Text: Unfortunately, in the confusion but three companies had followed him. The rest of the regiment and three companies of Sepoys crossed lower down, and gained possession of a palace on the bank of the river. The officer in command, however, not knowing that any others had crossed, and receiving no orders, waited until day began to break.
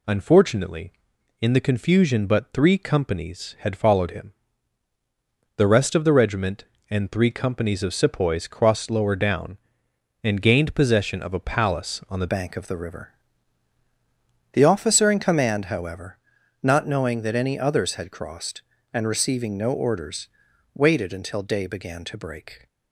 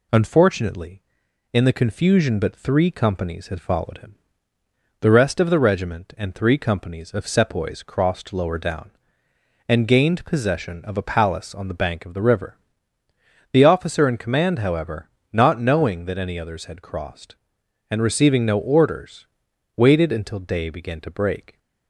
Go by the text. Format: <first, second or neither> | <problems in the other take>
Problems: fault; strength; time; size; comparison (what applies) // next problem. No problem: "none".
second | changes voice at "bank"; from 12.2 s on; 10.4 s long